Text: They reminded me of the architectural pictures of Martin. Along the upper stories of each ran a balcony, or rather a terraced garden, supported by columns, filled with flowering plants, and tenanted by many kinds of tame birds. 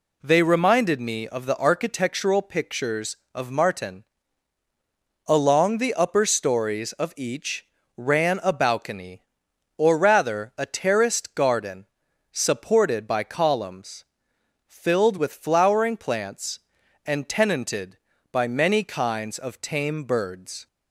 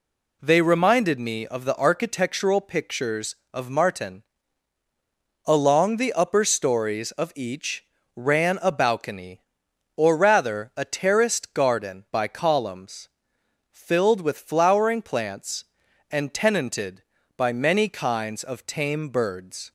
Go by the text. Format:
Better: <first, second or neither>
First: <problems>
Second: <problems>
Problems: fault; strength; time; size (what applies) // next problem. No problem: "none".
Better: first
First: pauses between "each" and "ran"; slight; at 7.6 s; 0.30 s long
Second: pauses between "each" and "ran"; slight; at 7.8 s; 0.30 s long // skips "supported"; at 12.0 s